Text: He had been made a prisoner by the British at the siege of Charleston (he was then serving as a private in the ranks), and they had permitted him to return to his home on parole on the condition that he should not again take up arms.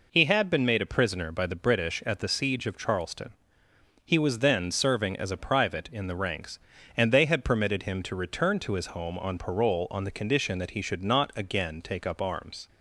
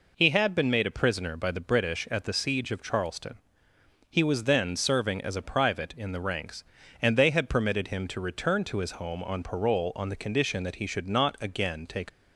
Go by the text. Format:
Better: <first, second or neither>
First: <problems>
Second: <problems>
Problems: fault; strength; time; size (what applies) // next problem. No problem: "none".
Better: first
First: none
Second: stops before "up arms"; at 12.0 s